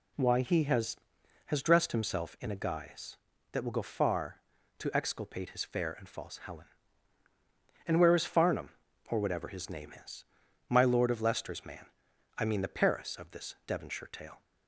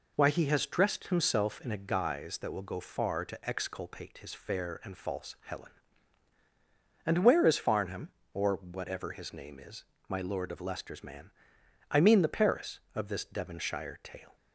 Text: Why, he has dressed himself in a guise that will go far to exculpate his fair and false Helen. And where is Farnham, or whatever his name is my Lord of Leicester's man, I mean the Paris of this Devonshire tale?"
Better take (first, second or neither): second